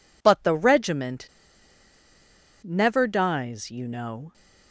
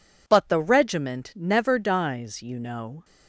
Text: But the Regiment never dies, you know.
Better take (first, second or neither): second